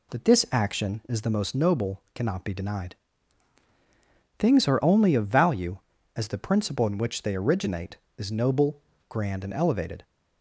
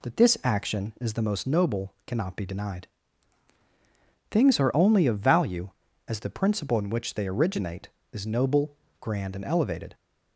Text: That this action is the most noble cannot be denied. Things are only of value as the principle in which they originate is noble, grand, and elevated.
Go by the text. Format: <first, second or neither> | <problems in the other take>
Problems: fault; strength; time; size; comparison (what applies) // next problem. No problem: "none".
neither | none